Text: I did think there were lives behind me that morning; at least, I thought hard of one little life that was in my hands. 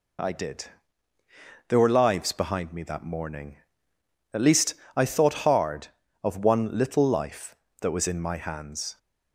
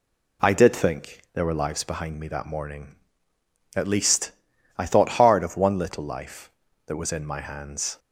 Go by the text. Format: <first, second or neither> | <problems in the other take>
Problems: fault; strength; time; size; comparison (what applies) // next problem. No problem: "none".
second | skips "think"; at 1.1 s